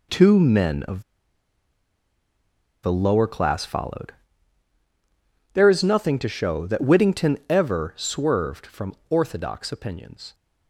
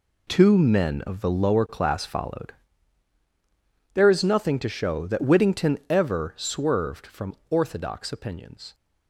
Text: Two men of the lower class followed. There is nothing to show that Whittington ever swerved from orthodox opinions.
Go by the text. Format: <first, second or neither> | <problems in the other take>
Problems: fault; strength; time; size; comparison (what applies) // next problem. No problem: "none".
second | pauses between "of" and "the"; strong; at 1.0 s; 1.8 s long // pauses between "from" and "orthodox"; slight; at 8.9 s; 0.16 s long; slight in the second